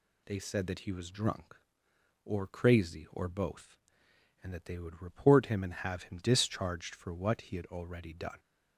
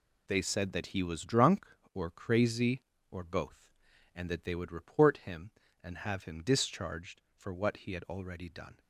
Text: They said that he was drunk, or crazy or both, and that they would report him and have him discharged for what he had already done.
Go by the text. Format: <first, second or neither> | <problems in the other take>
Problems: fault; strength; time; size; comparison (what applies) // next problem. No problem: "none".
first | gets quieter; strong; throughout; 8.5 dB